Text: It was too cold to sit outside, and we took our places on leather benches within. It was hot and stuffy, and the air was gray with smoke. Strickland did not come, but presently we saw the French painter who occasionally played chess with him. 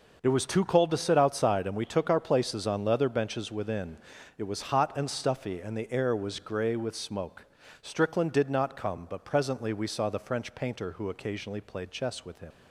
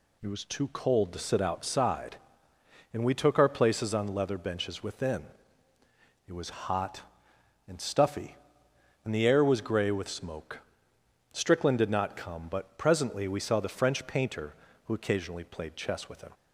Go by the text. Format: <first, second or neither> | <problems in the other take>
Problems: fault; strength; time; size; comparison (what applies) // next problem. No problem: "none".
second | leaves "him" unfinished; at 12.5 s; 45 ms